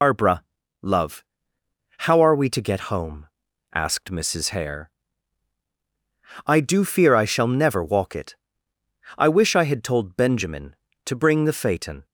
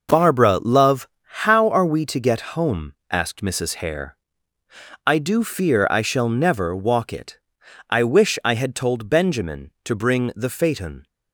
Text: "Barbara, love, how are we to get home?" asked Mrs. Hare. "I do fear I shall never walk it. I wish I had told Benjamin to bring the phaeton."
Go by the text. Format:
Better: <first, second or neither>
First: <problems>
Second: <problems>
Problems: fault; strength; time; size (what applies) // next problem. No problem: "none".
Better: second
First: loses the start of "Barbara"; at 0.0 s; 115 ms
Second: none